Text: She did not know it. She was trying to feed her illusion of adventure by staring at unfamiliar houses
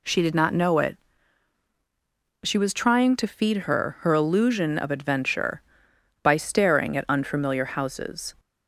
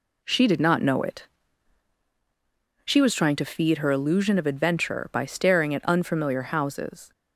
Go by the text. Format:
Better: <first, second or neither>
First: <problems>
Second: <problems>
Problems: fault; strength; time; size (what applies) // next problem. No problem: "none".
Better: second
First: says "her" twice; at 4.0 s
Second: none